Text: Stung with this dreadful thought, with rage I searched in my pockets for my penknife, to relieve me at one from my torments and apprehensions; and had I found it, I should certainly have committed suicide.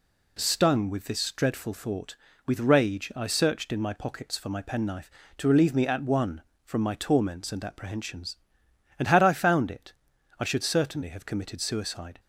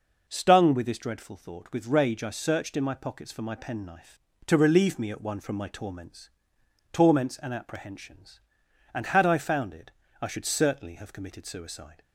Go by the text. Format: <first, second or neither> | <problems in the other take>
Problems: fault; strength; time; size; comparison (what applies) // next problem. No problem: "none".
first | says "torments" twice; at 6.9 s